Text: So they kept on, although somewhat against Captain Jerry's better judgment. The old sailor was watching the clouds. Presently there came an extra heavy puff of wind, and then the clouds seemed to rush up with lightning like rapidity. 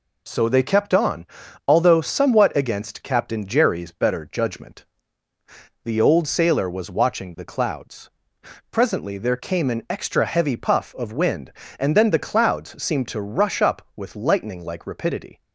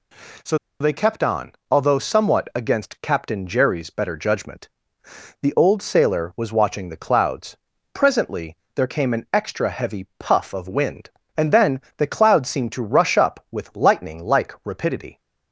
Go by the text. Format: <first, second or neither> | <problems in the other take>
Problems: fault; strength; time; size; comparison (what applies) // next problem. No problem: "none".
first | pauses between "So" and "they"; slight; at 0.5 s; 0.23 s long // pauses between "Presently" and "there"; slight; at 8.5 s; 0.18 s long // pauses between "then" and "the"; slight; at 11.7 s; 0.18 s long